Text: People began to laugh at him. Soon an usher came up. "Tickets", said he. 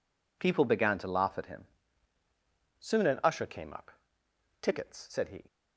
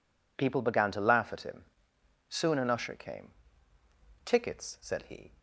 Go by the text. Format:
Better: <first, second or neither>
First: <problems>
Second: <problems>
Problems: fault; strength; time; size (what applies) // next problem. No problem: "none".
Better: first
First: none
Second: skips "up"; at 3.7 s